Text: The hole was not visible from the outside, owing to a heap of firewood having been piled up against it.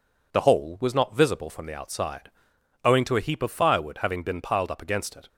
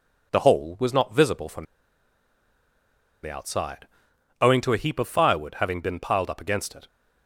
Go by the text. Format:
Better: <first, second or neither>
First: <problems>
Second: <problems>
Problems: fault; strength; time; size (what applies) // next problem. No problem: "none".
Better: first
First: none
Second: pauses between "from" and "the"; strong; at 1.6 s; 1.5 s long